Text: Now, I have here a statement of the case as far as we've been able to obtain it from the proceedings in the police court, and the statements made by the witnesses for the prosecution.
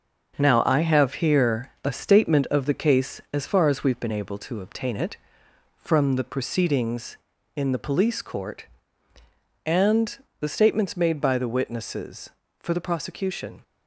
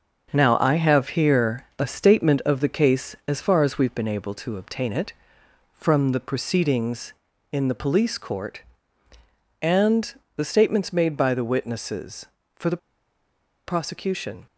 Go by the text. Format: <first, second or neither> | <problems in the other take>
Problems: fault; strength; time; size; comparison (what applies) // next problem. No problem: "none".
first | starts louder than the rest; until 1.3 s; 6.5 dB; also in the first // pauses between "and" and "the"; slight; at 10.1 s; 0.22 s long; slight in the first // pauses between "the" and "prosecution"; noticeable; at 12.7 s; 0.89 s long